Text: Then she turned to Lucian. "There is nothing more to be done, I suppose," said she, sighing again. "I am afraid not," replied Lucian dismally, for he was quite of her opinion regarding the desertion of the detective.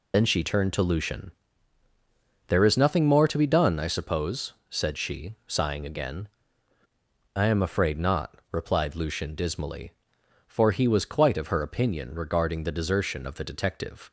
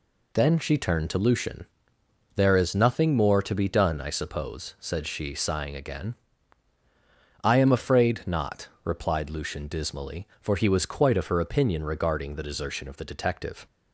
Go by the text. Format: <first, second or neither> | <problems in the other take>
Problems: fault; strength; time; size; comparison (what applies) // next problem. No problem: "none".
second | loses the start of "Then"; at 0.1 s; 55 ms